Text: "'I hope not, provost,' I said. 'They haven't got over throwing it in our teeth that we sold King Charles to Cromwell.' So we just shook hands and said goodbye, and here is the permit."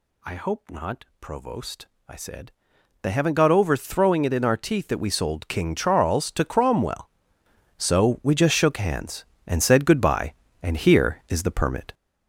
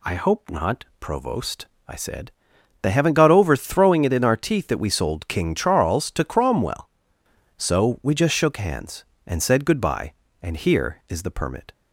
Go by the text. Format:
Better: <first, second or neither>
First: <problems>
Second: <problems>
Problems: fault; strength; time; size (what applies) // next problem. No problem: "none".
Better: second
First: gets louder; strong; throughout; 7 dB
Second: none